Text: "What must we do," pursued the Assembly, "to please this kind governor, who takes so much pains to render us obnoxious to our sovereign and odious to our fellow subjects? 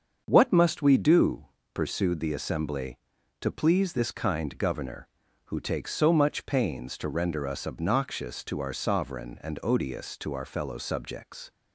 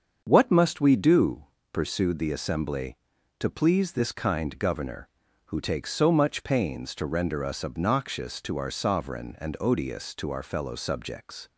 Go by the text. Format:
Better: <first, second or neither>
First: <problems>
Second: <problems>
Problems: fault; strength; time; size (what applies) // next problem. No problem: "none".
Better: neither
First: starts louder than the rest; until 1.2 s; 7 dB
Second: starts louder than the rest; until 1.2 s; 7 dB